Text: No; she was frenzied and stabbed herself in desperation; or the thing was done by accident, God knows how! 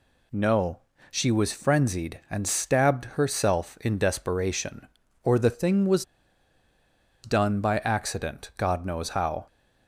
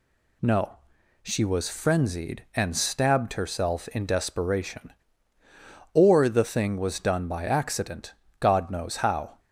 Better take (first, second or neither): second